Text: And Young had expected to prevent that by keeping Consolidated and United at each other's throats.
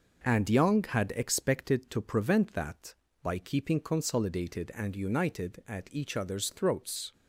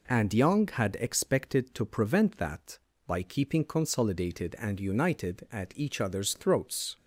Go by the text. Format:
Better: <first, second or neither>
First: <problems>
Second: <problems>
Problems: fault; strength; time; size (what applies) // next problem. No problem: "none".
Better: second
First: gets quieter; noticeable; throughout; 5 dB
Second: none